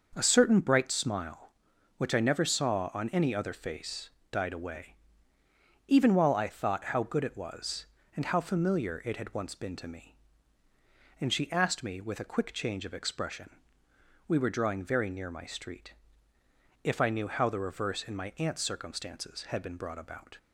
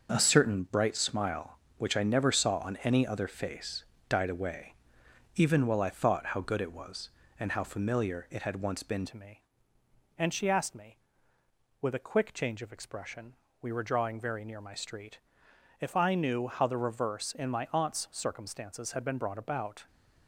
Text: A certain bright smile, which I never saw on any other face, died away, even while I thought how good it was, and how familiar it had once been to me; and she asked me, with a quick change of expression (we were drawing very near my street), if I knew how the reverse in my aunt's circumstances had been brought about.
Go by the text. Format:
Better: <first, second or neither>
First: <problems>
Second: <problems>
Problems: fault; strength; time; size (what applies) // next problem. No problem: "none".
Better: first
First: starts louder than the rest; until 1.1 s; 6 dB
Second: starts louder than the rest; until 1.1 s; 6 dB // changes voice at "to"; from 9.0 s on; 10.8 s long